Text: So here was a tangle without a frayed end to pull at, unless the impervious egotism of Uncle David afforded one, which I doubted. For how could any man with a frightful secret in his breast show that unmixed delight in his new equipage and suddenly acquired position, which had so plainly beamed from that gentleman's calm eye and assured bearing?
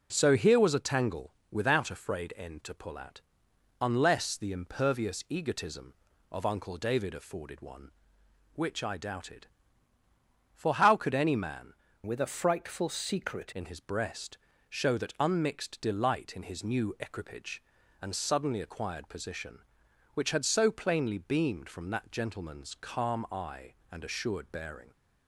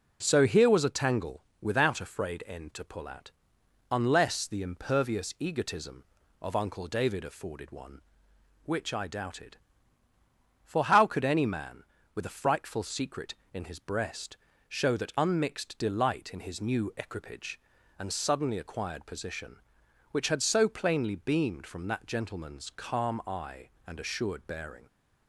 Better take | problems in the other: second | pauses between "tangle" and "without"; slight; at 1.3 s; 0.18 s long; slight in the second // changes voice from "with" to "secret"; from 12.0 to 13.5 s; 1.5 s long // pauses between "breast" and "show"; slight; at 14.3 s; 0.32 s long; slight in the second

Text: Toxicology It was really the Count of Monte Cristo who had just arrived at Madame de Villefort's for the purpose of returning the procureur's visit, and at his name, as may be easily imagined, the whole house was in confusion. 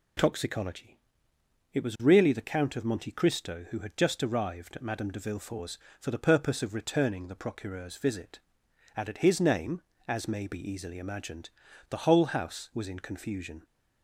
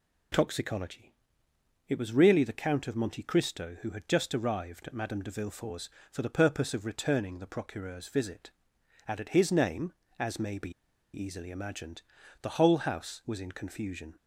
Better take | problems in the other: first | pauses between "Toxicology" and "It"; noticeable; at 1.1 s; 0.74 s long; noticeable in the first // pauses between "be" and "easily"; at 10.7 s; 0.42 s long

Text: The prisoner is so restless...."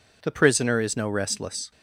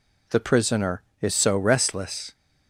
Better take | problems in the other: second | says "no" for "so"; at 0.9 s

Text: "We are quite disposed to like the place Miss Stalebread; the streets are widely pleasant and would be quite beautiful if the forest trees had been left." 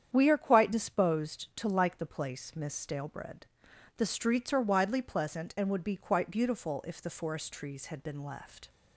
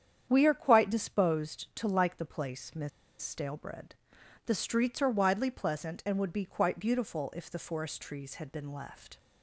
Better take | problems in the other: first | starts louder than the rest; strong; until 1.3 s; 8.5 dB; strong in the first // pauses between "Miss" and "Stalebread"; slight; at 2.8 s; 0.32 s long

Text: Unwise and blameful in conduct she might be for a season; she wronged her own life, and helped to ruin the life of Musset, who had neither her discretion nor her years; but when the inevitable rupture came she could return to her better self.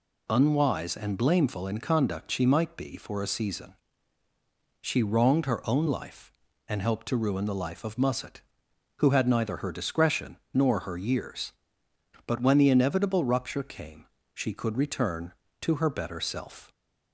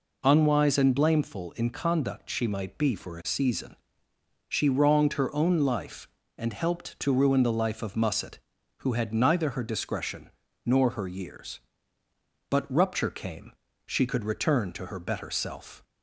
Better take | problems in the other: first | pauses between "discretion" and "nor"; slight; at 10.2 s; 0.34 s long; slight in the first // skips "when the inevitable"; at 12.7 s // pauses between "came" and "she"; slight; at 13.5 s; 0.34 s long; slight in the first

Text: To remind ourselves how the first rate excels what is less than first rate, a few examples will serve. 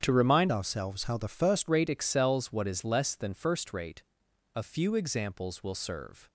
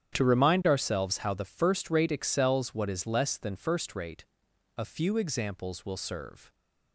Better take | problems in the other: second | starts louder than the rest; strong; until 1.0 s; 8.5 dB; strong in the second // changes voice from "ourselves" to "first"; from 0.5 to 1.6 s; 1.1 s long

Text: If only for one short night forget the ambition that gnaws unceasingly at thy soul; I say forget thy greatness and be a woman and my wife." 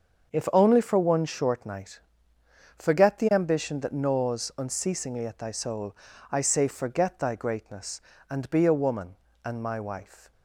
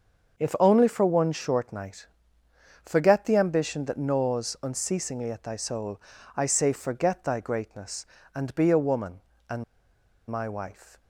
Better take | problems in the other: first | starts louder than the rest; until 1.4 s; 6.5 dB; also in the first // pauses between "night" and "forget"; noticeable; at 2.0 s; 0.76 s long; noticeable in the first // pauses between "and" and "my"; noticeable; at 9.6 s; 0.65 s long

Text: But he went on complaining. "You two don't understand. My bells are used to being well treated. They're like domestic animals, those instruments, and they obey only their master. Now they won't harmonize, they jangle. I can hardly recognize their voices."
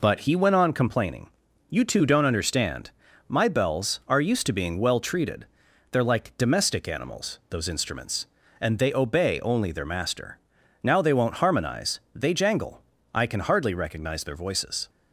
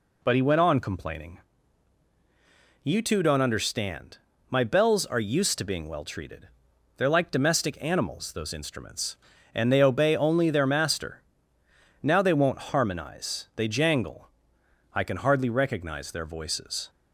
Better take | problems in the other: neither | none

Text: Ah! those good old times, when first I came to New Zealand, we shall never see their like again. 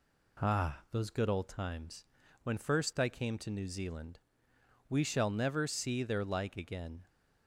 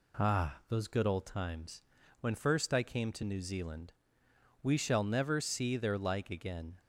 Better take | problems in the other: neither | none

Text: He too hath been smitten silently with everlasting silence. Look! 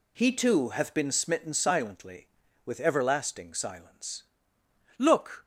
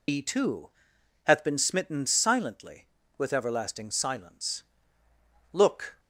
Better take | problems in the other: first | loses the start of "He"; at 0.0 s; 95 ms // pauses between "too" and "hath"; noticeable; at 0.6 s; 0.54 s long

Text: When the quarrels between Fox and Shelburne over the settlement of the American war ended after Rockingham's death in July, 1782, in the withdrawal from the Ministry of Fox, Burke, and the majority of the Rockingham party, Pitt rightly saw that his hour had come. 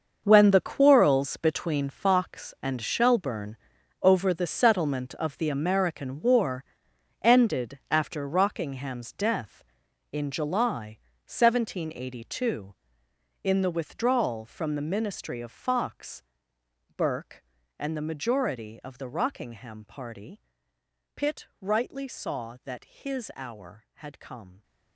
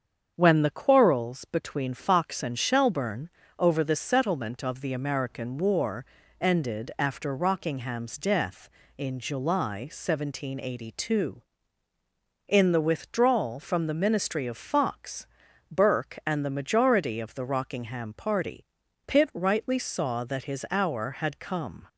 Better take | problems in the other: second | gets quieter; strong; throughout; 12.5 dB // starts louder than the rest; until 1.2 s; 6.5 dB; strong in the second // pauses between "Shelburne" and "over"; at 3.5 s; 0.44 s long; slight in the second // pauses between "war" and "ended"; noticeable; at 6.6 s; 0.56 s long; slight in the second

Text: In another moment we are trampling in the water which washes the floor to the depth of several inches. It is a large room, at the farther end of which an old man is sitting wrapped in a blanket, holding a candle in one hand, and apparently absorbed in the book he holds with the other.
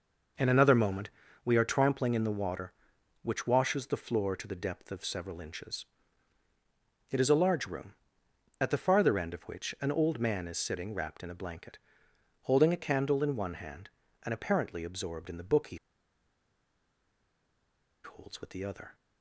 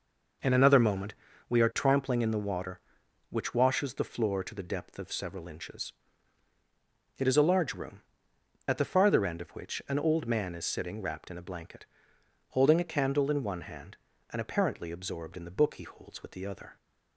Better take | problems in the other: second | pauses between "moment" and "we"; slight; at 1.1 s; 0.34 s long; slight in the second // pauses between "he" and "holds"; strong; at 15.7 s; 2.2 s long

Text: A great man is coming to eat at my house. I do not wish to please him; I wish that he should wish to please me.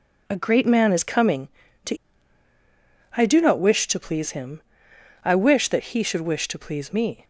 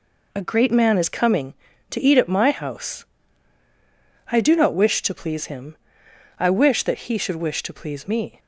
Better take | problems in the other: second | skips "eat at my house"; at 2.5 s

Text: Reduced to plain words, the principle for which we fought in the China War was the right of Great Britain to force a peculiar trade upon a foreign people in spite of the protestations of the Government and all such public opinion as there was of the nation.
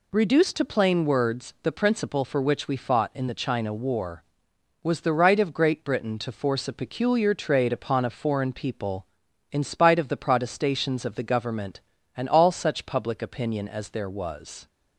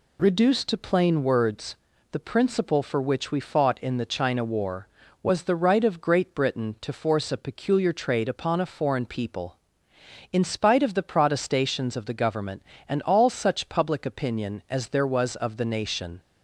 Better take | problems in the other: second | stops before "of the nation"; at 14.6 s

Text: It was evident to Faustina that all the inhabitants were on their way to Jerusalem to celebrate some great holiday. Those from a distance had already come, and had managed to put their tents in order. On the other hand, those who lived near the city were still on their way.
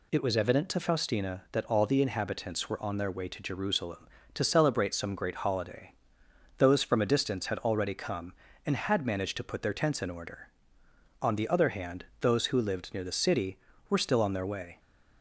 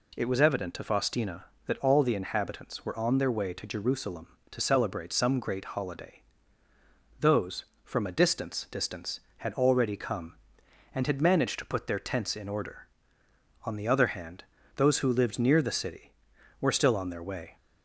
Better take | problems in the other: first | says "distance" twice; at 8.6 s

